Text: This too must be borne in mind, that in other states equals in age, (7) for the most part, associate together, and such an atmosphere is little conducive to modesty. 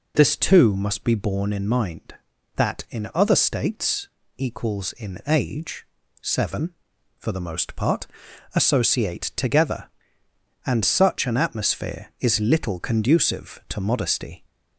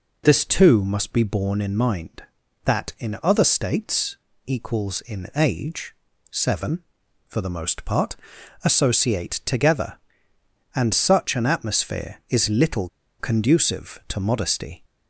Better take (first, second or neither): first